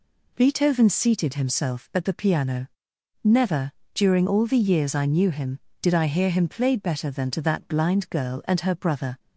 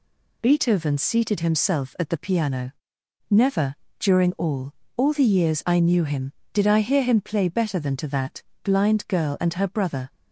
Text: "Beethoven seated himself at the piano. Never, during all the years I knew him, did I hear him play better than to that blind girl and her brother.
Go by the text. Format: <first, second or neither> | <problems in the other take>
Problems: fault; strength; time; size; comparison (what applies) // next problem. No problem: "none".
first | says "all" twice; at 4.9 s // pauses between "that" and "blind"; slight; at 8.4 s; 0.22 s long